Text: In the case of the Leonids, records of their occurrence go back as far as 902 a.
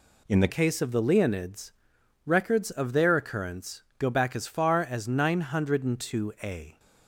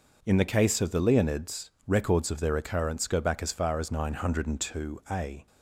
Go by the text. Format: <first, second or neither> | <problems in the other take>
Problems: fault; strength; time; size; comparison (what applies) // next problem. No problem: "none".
second | changes voice at "case"; from 0.4 s on; 6.3 s long // pauses between "occurrence" and "go"; slight; at 3.8 s; 0.18 s long